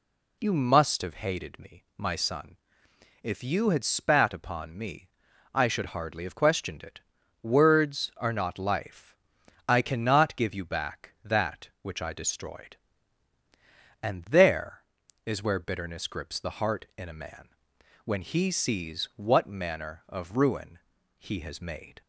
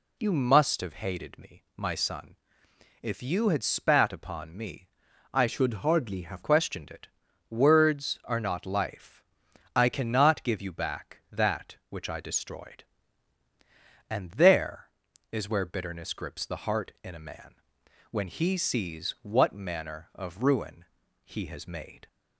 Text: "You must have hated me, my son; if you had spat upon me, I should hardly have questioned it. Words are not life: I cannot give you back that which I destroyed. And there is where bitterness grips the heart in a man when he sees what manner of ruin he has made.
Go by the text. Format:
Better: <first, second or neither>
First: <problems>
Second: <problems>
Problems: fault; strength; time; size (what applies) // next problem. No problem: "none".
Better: first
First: pauses between "man" and "when"; noticeable; at 17.4 s; 0.56 s long // pauses between "ruin" and "he"; at 20.7 s; 0.40 s long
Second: changes voice from "should" to "have"; from 5.4 to 6.4 s; 1.0 s long // pauses between "man" and "when"; noticeable; at 17.5 s; 0.56 s long // pauses between "ruin" and "he"; at 20.8 s; 0.40 s long